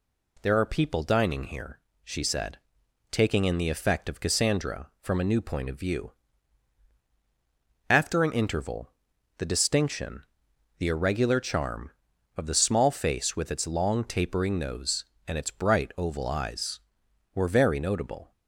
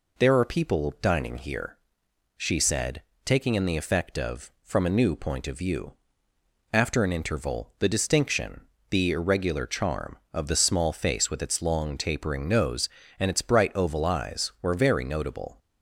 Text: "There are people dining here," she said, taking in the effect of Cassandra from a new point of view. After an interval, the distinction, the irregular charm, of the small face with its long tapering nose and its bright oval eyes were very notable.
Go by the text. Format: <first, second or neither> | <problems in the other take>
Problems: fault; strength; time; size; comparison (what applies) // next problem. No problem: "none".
first | skips "Cassandra"; at 4.5 s